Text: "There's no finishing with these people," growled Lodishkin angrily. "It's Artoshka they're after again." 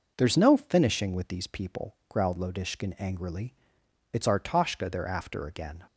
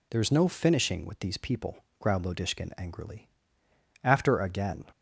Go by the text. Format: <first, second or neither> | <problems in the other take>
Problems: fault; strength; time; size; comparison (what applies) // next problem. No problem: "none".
first | skips "It's Artoshka they're"; at 3.6 s